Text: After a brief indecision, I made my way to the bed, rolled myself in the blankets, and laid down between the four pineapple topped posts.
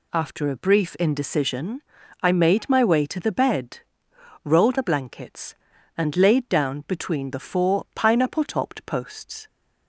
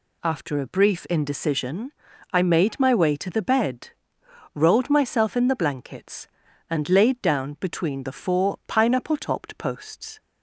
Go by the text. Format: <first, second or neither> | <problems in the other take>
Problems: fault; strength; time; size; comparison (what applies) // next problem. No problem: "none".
second | skips "myself in"; at 4.7 s